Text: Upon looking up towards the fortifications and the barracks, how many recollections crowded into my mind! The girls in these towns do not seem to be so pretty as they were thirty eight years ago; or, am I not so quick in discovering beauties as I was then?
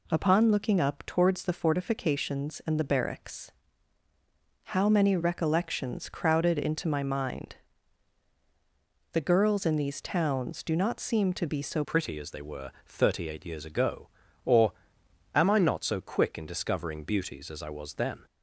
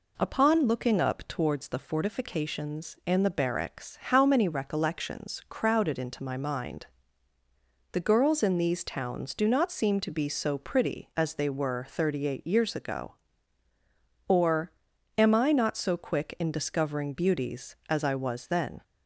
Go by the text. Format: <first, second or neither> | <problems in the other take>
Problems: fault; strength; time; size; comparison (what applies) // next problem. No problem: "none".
second | changes voice at "pretty"; from 11.8 s on; 6.4 s long // pauses between "were" and "thirty"; slight; at 12.7 s; 0.16 s long